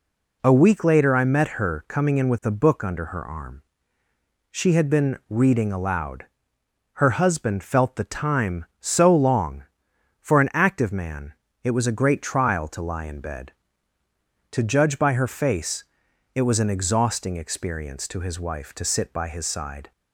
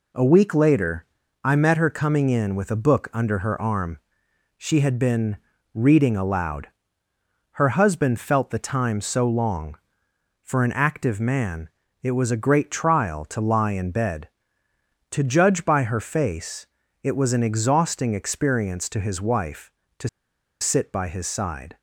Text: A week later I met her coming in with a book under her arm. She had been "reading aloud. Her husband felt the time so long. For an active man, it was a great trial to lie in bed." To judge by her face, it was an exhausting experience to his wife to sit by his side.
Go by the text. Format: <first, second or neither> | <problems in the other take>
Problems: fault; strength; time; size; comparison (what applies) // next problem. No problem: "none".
first | pauses between "later" and "I"; at 1.0 s; 0.40 s long // pauses between "been" and "reading"; at 5.3 s; 0.38 s long // pauses between "to" and "sit"; noticeable; at 20.0 s; 0.52 s long